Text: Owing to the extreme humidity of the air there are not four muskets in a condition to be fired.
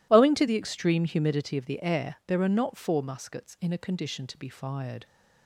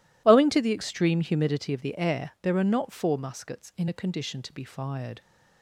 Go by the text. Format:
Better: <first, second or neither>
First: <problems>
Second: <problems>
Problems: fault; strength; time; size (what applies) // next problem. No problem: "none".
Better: neither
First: none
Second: none